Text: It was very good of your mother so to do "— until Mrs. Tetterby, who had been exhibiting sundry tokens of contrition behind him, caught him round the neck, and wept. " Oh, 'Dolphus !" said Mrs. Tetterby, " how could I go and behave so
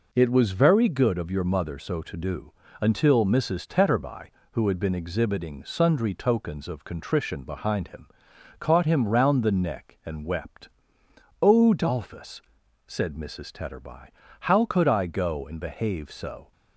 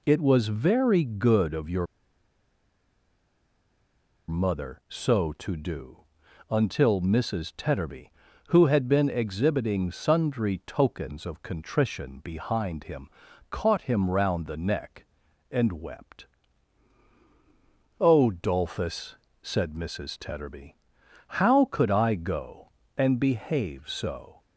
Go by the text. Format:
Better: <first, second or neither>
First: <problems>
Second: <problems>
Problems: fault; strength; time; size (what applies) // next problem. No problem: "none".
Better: first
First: none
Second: pauses between "your" and "mother"; strong; at 1.8 s; 2.4 s long